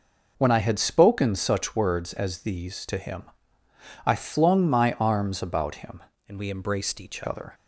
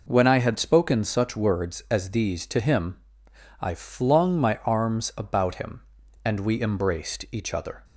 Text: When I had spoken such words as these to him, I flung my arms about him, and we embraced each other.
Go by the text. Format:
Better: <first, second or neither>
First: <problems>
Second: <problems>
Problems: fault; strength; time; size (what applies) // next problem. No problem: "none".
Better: second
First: changes voice from "and" to "each"; from 6.2 to 7.2 s; 1.0 s long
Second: none